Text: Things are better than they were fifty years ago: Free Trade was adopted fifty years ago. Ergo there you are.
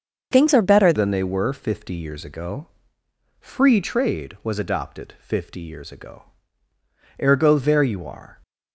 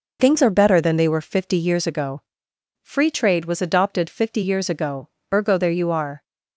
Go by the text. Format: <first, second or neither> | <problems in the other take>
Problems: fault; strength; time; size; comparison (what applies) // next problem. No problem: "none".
second | starts louder than the rest; until 1.3 s; 6.5 dB // changes voice at "than"; from 0.9 s on; 7.5 s long